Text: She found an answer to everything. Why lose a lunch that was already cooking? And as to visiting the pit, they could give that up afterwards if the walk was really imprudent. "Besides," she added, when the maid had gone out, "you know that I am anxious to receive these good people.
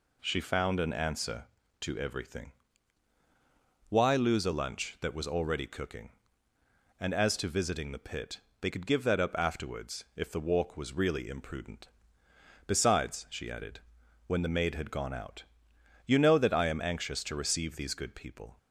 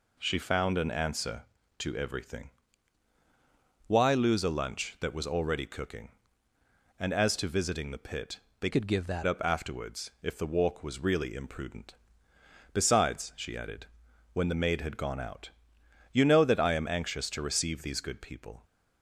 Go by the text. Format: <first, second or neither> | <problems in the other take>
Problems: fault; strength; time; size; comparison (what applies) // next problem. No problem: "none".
first | changes voice from "could" to "that"; from 8.7 to 9.2 s; 0.5 s long